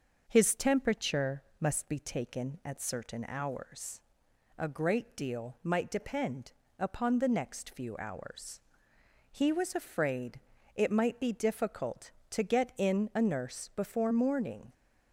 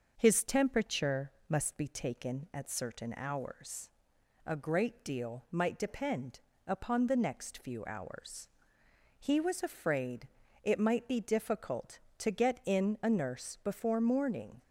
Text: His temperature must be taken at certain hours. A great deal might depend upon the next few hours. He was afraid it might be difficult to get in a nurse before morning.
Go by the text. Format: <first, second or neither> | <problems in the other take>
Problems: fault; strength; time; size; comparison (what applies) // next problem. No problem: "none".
neither | starts louder than the rest; noticeable; the same in both // pauses between "temperature" and "must"; slight; the same in both // pauses between "depend" and "upon"; slight; the same in both // pauses between "afraid" and "it"; slight; the same in both